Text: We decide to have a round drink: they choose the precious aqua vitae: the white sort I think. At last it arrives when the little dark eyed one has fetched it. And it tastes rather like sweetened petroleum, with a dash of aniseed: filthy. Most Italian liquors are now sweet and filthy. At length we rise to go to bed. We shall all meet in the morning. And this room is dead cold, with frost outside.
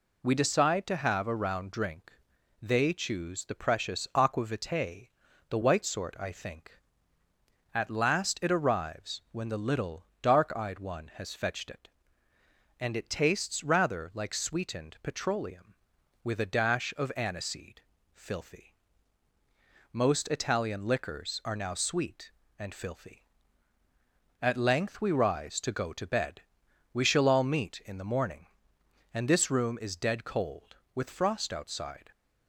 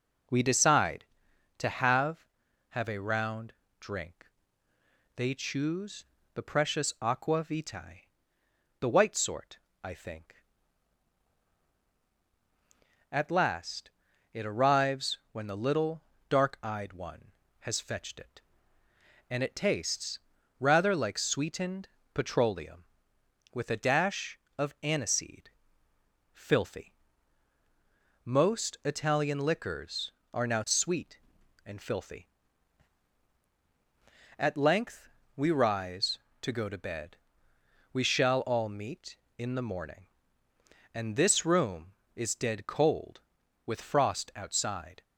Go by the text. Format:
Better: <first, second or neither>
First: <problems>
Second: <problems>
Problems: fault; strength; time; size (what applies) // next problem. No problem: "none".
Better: first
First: pauses between "little" and "dark"; slight; at 10.0 s; 0.16 s long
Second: says "have" twice; at 2.6 s // pauses between "round" and "drink"; slight; at 3.5 s; 0.28 s long // pauses between "choose" and "the"; slight; at 6.0 s; 0.30 s long // pauses between "sort" and "I"; slight; at 9.5 s; 0.26 s long // pauses between "last" and "it"; at 13.9 s; 0.42 s long // pauses between "little" and "dark"; slight; at 16.0 s; 0.26 s long // pauses between "tastes" and "rather"; at 20.1 s; 0.42 s long // pauses between "sweetened" and "petroleum"; slight; at 21.8 s; 0.26 s long // pauses between "length" and "we"; slight; at 35.0 s; 0.28 s long